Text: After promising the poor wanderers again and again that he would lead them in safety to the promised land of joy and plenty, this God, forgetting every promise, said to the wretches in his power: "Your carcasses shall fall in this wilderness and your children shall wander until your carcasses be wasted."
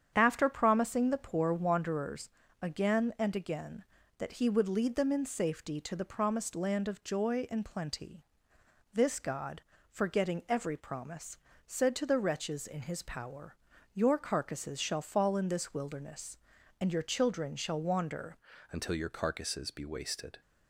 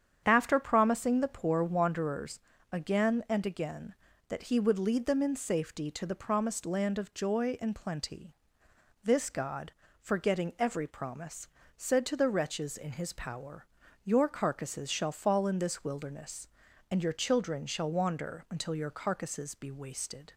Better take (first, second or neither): second